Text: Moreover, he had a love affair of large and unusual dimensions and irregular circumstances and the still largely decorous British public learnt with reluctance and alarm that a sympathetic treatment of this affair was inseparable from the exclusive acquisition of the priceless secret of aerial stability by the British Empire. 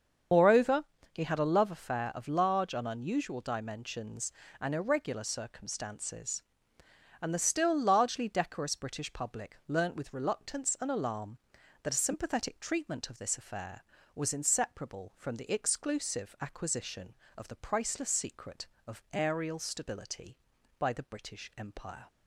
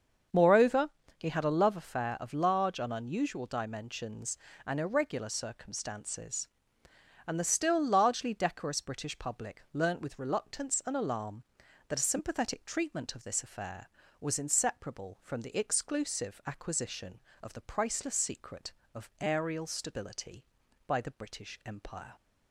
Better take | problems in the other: second | loses the start of "Moreover"; at 0.3 s; 45 ms // starts louder than the rest; until 1.6 s; 7 dB; also in the second

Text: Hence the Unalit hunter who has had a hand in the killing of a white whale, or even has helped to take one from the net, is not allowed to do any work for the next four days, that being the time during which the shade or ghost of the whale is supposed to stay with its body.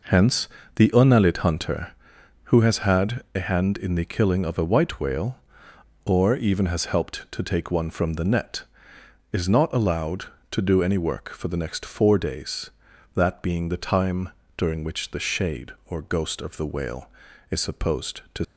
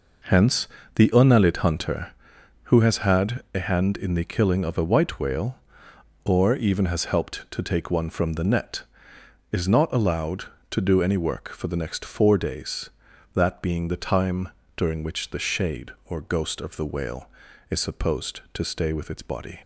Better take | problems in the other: second | pauses between "Hence" and "the"; slight; at 0.4 s; 0.26 s long; slight in the second // pauses between "time" and "during"; slight; at 14.2 s; 0.28 s long; slight in the second // stops before "stay with its body"; at 18.4 s

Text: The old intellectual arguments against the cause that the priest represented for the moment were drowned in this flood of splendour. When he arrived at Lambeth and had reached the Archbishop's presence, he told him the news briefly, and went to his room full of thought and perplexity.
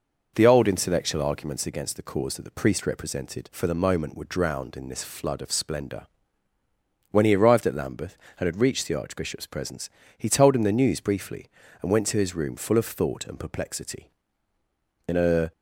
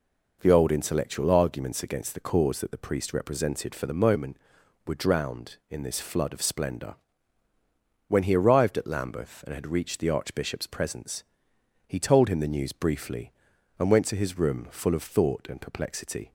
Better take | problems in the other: second | goes on to say "In a"; slight; from 15.0 s on; 0.44 s long

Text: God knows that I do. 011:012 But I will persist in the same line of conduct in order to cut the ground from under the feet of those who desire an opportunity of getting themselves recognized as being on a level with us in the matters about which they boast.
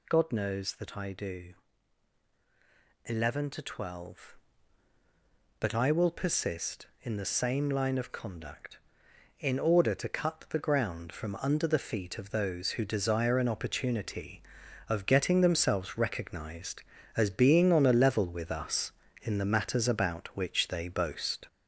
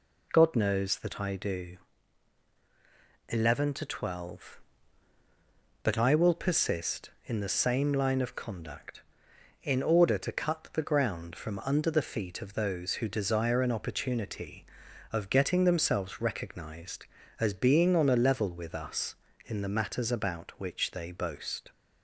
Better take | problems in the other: second | gets louder; noticeable; throughout; 4.5 dB

